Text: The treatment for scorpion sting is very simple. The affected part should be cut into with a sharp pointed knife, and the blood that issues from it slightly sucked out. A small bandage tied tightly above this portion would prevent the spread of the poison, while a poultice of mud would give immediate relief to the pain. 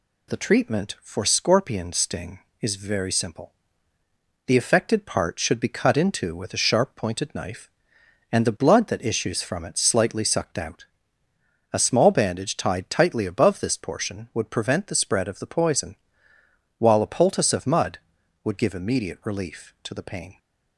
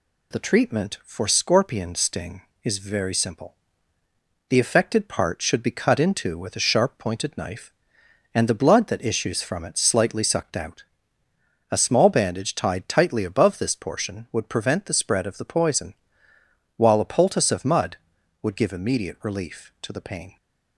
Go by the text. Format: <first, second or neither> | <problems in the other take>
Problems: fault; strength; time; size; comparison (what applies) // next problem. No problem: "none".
neither | none